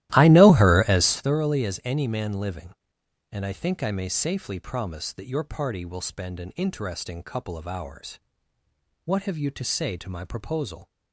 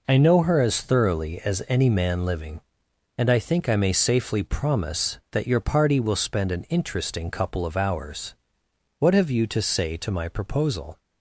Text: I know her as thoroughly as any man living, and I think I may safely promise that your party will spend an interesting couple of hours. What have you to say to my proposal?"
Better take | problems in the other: second | starts louder than the rest; strong; until 1.3 s; 15 dB

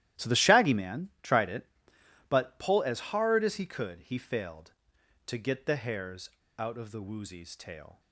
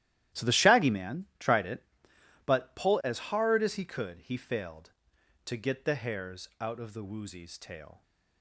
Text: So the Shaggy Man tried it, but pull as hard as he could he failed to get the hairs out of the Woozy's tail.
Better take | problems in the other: second | starts louder than the rest; strong; until 1.3 s; 13 dB; strong in the second // pauses between "hairs" and "out"; slight; at 6.2 s; 0.28 s long

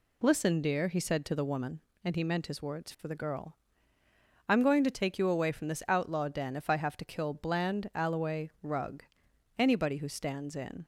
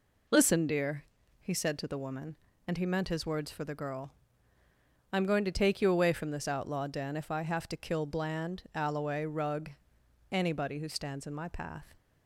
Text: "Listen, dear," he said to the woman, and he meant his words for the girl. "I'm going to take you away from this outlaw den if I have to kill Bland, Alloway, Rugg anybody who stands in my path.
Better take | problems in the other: second | pauses between "Rugg" and "anybody"; noticeable; at 9.0 s; 0.52 s long; noticeable in the second // stops before "my path"; at 10.8 s

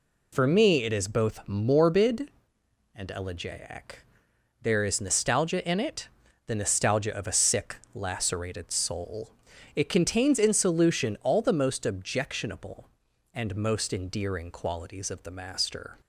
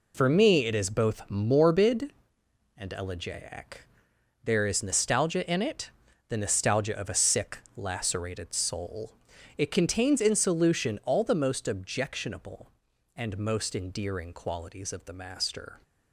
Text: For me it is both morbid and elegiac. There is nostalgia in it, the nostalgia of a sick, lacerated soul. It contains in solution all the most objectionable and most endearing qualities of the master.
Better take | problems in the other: first | gets quieter; strong; throughout; 9 dB

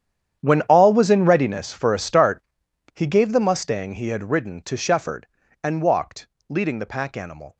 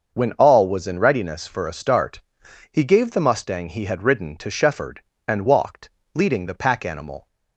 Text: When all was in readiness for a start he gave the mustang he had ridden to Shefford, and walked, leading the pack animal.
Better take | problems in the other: second | gets quieter; strong; throughout; 17.5 dB // starts louder than the rest; strong; until 1.4 s; 9.5 dB; also in the second // pauses between "start" and "he"; noticeable; at 2.4 s; 0.54 s long; noticeable in the second

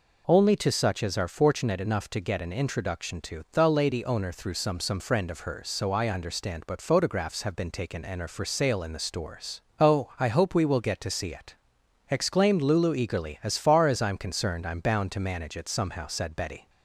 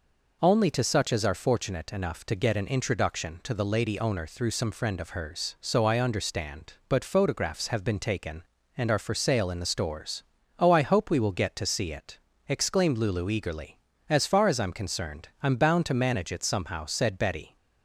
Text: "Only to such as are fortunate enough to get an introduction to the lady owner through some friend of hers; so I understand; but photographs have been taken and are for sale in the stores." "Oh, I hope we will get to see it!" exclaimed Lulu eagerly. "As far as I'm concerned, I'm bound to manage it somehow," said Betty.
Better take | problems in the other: second | says "some" twice; at 4.7 s

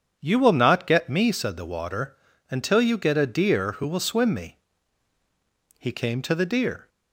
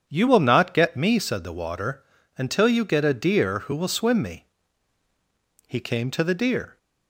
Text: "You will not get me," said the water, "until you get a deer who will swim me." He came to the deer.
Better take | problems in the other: neither | starts louder than the rest; strong; the same in both

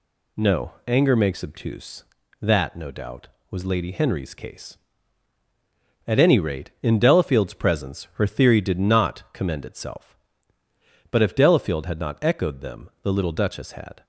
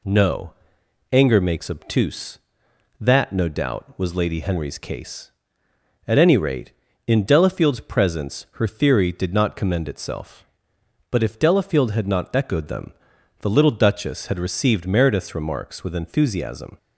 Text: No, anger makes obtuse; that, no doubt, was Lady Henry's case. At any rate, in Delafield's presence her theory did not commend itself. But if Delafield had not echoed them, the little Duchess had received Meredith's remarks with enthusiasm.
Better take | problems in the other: second | stops before "received Meredith's remarks with enthusiasm"; at 14.0 s

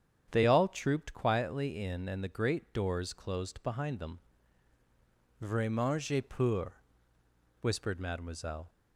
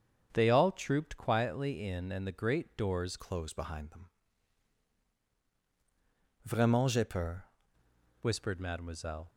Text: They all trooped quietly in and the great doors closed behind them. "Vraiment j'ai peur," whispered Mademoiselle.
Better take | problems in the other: first | starts louder than the rest; strong; until 1.3 s; 7 dB; strong in the first // changes voice from "closed" to "peur"; from 3.1 to 7.4 s; 4.3 s long

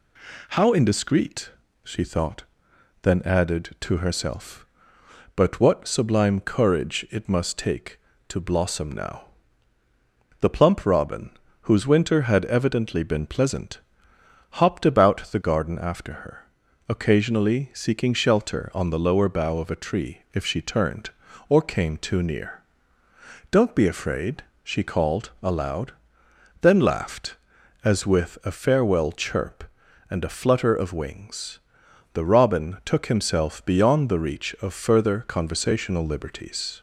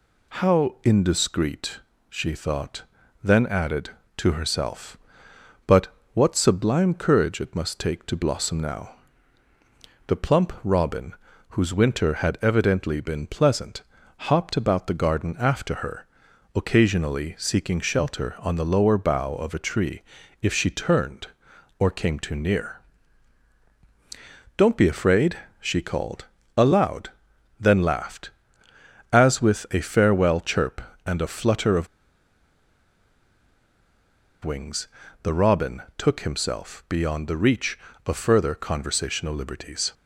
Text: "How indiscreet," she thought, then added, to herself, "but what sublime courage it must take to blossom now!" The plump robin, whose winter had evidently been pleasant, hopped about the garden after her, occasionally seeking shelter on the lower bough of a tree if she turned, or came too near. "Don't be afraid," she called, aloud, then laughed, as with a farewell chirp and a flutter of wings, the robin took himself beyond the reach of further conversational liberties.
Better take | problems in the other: first | pauses between "but" and "what"; slight; at 5.8 s; 0.24 s long // pauses between "tree" and "if"; at 20.0 s; 0.40 s long // pauses between "of" and "wings"; strong; at 31.8 s; 2.5 s long // pauses between "robin" and "took"; slight; at 35.8 s; 0.16 s long

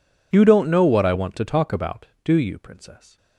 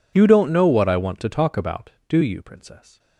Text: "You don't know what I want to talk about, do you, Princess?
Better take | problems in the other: neither | none

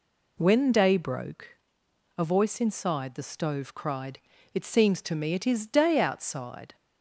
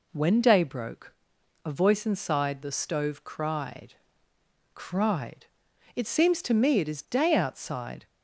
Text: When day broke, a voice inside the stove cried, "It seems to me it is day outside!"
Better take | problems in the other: first | says "cried" twice; at 4.7 s

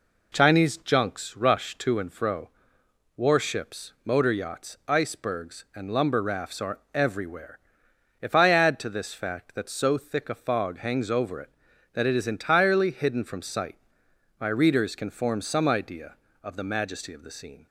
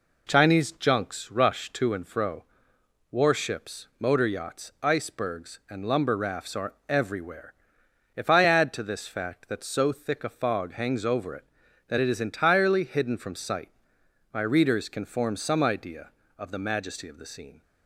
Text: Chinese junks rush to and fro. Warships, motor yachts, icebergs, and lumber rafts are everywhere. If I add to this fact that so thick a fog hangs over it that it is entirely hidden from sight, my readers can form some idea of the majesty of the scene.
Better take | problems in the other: neither | none

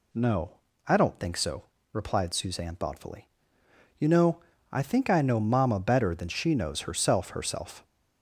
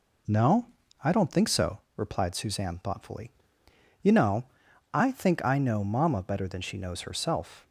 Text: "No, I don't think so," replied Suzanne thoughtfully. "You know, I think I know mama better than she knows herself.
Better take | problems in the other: second | says "herself" twice; at 7.2 s

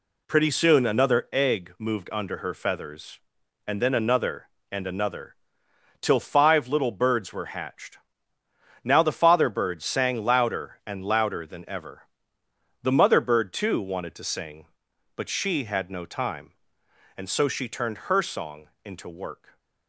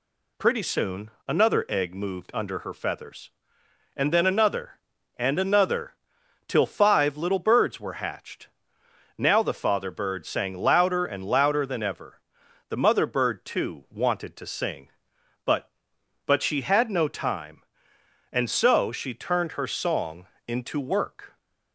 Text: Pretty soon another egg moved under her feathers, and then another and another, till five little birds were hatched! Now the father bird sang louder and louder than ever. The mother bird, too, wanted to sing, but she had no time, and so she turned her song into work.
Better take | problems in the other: first | pauses between "soon" and "another"; slight; at 1.0 s; 0.18 s long // says "but" twice; at 16.2 s // pauses between "song" and "into"; slight; at 20.2 s; 0.20 s long; slight in the first

